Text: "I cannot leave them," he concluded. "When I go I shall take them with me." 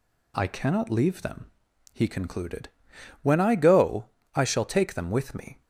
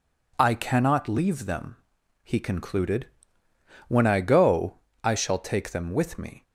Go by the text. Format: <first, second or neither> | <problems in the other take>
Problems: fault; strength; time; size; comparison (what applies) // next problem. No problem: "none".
neither | pauses between "go" and "I"; slight; the same in both